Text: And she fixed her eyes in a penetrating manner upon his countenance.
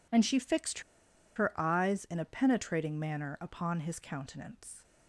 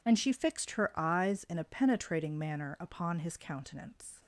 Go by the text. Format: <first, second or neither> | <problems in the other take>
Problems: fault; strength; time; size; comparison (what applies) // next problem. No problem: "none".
second | pauses between "fixed" and "her"; noticeable; at 0.7 s; 0.55 s long